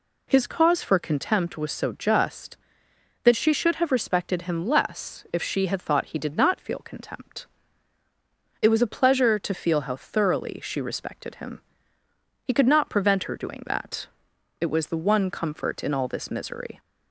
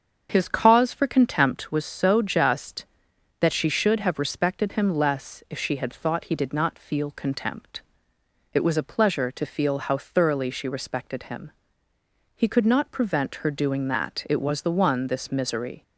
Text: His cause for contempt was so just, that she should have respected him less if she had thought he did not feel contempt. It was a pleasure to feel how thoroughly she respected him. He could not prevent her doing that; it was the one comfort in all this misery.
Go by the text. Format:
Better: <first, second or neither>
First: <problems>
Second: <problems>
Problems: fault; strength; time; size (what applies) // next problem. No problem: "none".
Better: first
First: none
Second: starts louder than the rest; until 1.3 s; 7 dB // skips "comfort in all"; at 15.0 s